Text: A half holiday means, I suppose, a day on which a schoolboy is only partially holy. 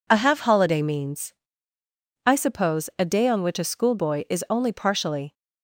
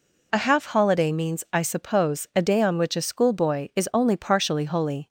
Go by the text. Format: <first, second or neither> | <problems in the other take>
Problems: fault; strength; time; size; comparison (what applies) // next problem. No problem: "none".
second | stops before "holy"; at 5.3 s